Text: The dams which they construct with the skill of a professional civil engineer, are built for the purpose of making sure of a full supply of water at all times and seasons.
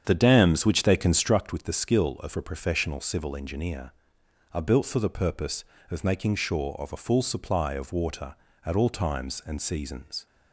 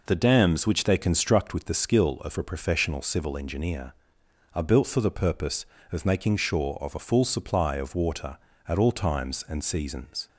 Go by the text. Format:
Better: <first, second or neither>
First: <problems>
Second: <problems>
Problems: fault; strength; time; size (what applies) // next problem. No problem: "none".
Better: second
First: starts louder than the rest; strong; until 1.3 s; 8 dB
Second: none